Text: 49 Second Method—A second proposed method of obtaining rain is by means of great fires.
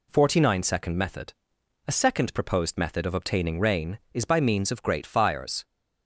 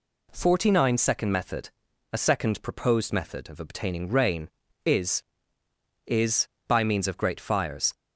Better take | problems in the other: first | says "is" twice; at 6.0 s

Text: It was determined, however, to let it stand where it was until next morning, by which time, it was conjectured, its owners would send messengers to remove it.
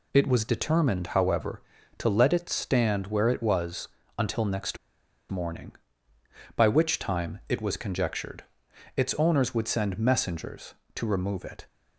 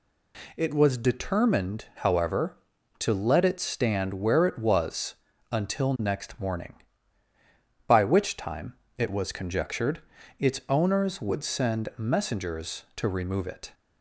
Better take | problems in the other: second | pauses between "was" and "until"; slight; at 3.8 s; 0.30 s long; also in the second // pauses between "next" and "morning"; noticeable; at 4.7 s; 0.52 s long

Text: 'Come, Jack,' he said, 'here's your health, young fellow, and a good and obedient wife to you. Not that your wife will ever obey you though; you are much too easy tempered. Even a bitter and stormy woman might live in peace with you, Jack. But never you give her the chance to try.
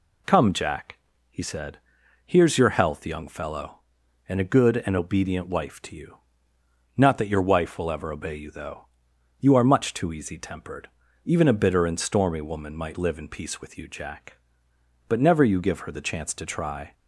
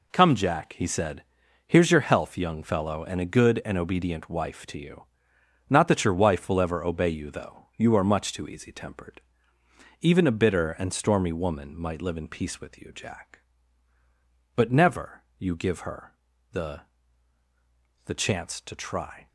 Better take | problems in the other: first | pauses between "her" and "the"; at 16.1 s; 0.38 s long // says "the" twice; at 18.0 s

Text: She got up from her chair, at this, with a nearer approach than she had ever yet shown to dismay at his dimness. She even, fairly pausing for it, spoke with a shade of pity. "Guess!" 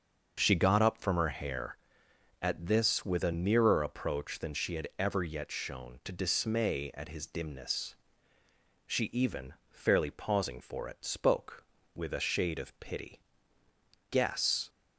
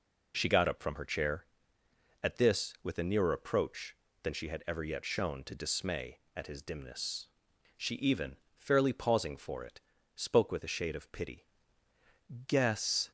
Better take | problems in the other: second | starts louder than the rest; until 1.3 s; 6.5 dB // says "hair" for "chair"; at 1.2 s

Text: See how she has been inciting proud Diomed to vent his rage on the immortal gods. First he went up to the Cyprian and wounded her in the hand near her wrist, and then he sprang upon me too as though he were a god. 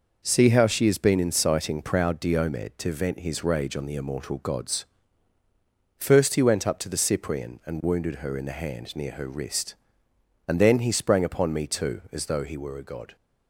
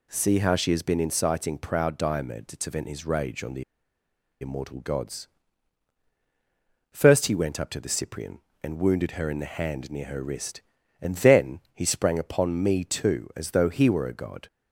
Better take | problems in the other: first | pauses between "the" and "immortal"; noticeable; at 3.6 s; 0.77 s long // pauses between "then" and "he"; slight; at 11.5 s; 0.16 s long

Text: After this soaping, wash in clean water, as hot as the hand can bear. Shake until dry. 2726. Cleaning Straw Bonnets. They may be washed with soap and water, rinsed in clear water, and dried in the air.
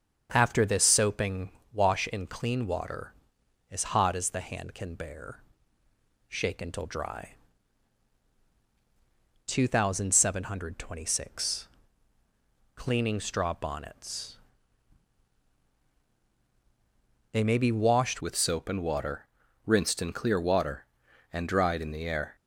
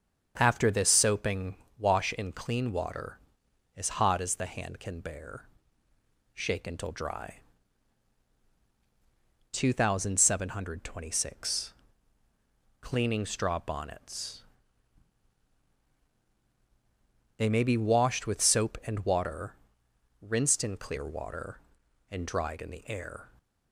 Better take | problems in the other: second | starts louder than the rest; until 1.3 s; 7 dB; also in the second // changes voice at "with"; from 18.1 s on; 4.2 s long

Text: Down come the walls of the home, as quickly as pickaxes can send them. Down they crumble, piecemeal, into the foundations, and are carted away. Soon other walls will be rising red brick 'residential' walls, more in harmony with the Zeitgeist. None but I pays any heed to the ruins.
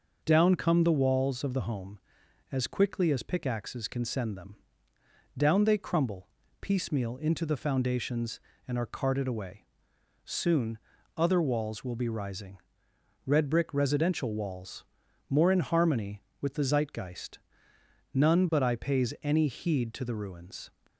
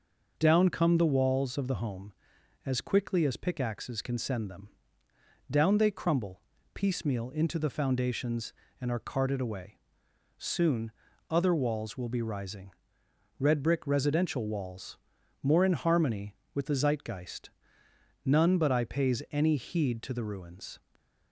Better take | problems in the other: neither | pauses between "Soon" and "other"; the same in both // pauses between "rising" and "red"; noticeable; the same in both

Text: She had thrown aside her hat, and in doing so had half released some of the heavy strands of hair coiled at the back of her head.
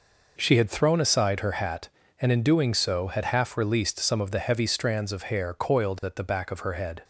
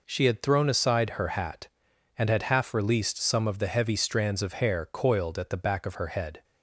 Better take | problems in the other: first | skips "in doing so"; at 2.2 s

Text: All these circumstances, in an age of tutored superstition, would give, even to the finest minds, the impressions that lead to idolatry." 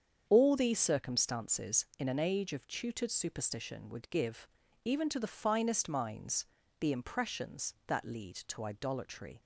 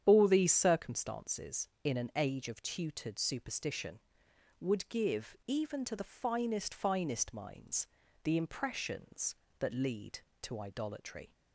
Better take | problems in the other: first | starts louder than the rest; strong; until 1.0 s; 9 dB; strong in the first // says "finest" twice; at 6.7 s

